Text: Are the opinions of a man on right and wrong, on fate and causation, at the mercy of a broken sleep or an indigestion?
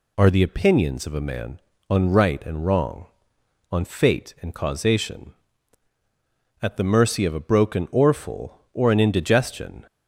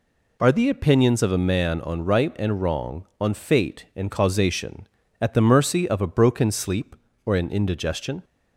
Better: second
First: says "orful" for "sleep"; at 7.8 s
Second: none

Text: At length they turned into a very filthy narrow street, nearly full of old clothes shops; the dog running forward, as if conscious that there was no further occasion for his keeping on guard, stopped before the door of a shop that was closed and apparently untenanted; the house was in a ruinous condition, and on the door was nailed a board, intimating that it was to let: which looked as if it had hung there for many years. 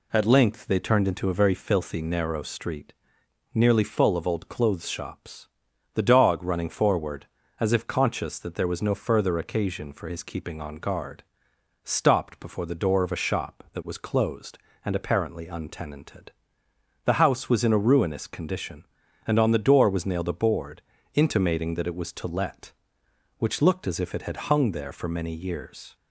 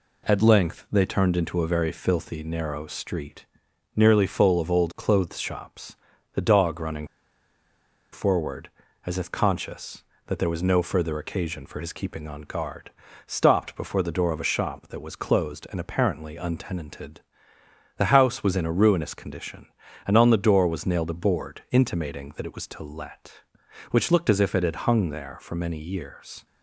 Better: first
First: none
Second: pauses between "running" and "forward"; at 7.0 s; 1.0 s long

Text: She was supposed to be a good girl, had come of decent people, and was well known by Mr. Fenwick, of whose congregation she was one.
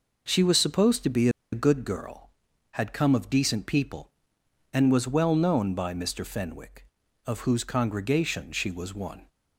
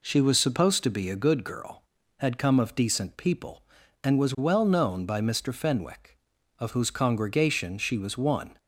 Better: second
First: pauses between "be" and "a"; slight; at 1.2 s; 0.23 s long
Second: none

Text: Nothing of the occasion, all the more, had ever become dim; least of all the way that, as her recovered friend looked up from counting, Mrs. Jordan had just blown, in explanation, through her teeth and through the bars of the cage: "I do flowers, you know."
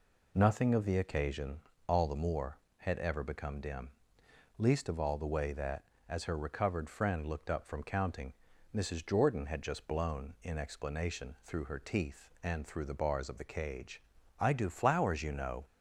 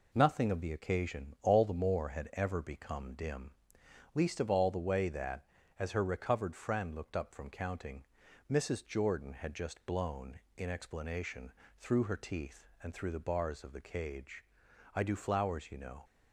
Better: neither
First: none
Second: none

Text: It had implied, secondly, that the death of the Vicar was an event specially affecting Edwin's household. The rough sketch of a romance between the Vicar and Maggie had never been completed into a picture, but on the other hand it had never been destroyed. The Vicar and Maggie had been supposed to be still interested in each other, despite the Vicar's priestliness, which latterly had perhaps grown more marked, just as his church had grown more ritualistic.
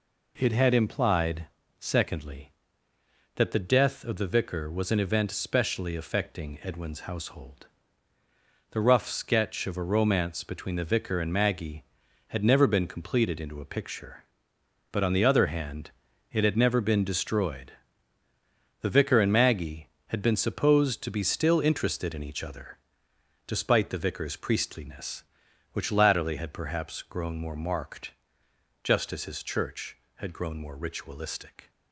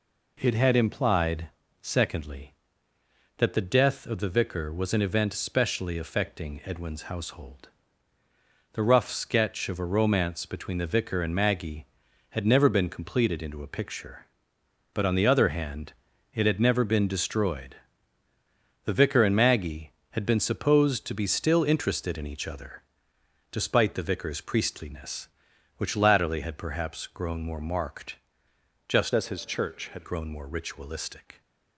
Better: first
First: pauses between "hand" and "it"; at 15.9 s; 0.40 s long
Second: pauses between "hand" and "it"; at 15.9 s; 0.40 s long // changes voice from "as" to "had"; from 29.1 to 30.0 s; 0.9 s long

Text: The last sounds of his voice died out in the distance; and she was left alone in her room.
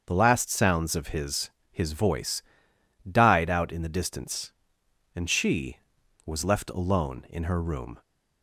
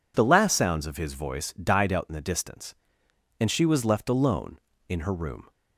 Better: second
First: starts louder than the rest; until 1.0 s; 6.5 dB // says "his" twice; at 1.7 s // pauses between "voice" and "died"; noticeable; at 2.4 s; 0.68 s long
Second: none

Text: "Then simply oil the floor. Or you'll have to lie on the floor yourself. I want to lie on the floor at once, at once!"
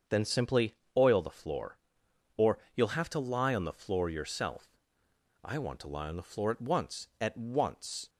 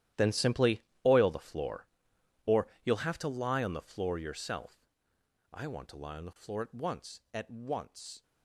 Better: first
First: starts louder than the rest; until 1.2 s; 7 dB // pauses between "simply" and "oil"; slight; at 0.7 s; 0.20 s long // pauses between "Or" and "you'll"; slight; at 2.5 s; 0.16 s long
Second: gets quieter; strong; throughout; 15 dB // starts louder than the rest; strong; until 1.3 s; 12.5 dB // pauses between "simply" and "oil"; slight; at 0.8 s; 0.22 s long // pauses between "Or" and "you'll"; slight; at 2.6 s; 0.16 s long

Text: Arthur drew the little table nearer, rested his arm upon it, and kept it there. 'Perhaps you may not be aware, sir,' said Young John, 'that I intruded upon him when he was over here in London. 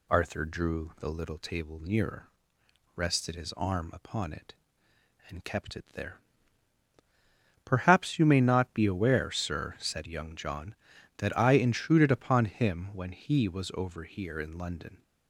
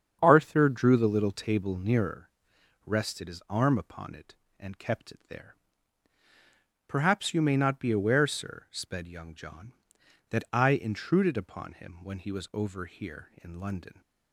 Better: first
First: none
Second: starts louder than the rest; strong; until 1.2 s; 7.5 dB // says "sped" for "said"; at 8.7 s

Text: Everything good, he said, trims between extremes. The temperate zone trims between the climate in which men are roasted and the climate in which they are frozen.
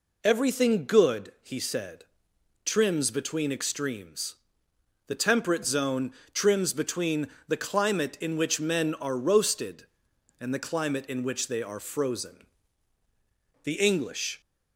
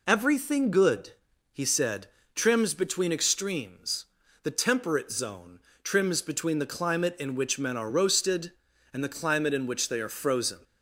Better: second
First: pauses between "zone" and "trims"; slight; at 6.1 s; 0.22 s long // pauses between "between" and "the"; slight; at 7.2 s; 0.20 s long // goes on to say "The English"; noticeable; from 13.6 s on; 0.76 s long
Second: pauses between "zone" and "trims"; slight; at 5.6 s; 0.24 s long

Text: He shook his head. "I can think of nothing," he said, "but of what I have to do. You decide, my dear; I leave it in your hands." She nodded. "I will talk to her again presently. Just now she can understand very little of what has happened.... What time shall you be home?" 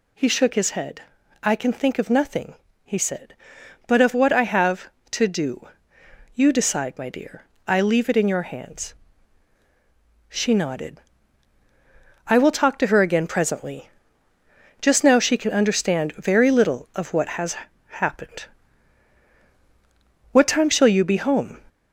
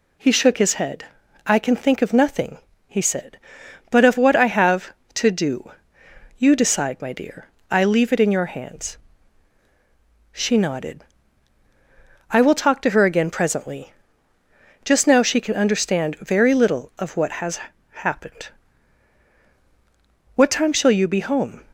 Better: second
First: gets louder; throughout; 3.5 dB // pauses between "has" and "happened"; slight; at 17.5 s; 0.32 s long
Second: pauses between "has" and "happened"; slight; at 17.6 s; 0.32 s long

